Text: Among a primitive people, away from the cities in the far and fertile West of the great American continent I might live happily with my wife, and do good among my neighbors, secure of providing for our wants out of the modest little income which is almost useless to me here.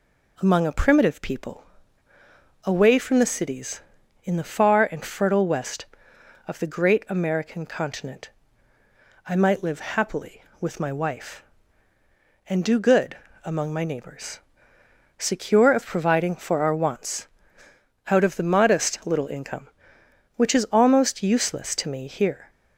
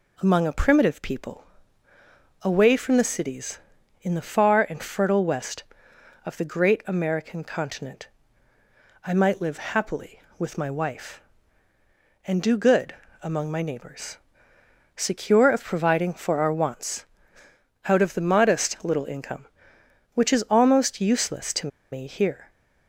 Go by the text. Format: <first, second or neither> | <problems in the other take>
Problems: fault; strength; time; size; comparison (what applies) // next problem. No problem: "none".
first | pauses between "continent" and "I"; noticeable; at 8.0 s; 0.96 s long; noticeable in the first // pauses between "good" and "among"; slight; at 12.9 s; 0.26 s long; slight in the first // pauses between "wants" and "out"; noticeable; at 17.0 s; 0.80 s long; noticeable in the first // pauses between "to" and "me"; slight; at 21.6 s; 0.24 s long